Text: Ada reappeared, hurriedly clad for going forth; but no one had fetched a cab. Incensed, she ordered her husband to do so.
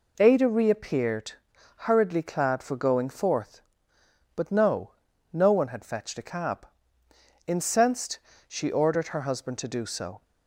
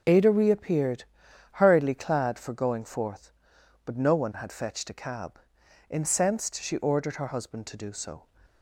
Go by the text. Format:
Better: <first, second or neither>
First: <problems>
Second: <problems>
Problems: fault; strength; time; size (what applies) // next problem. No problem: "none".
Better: second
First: says "no" twice; at 5.3 s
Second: none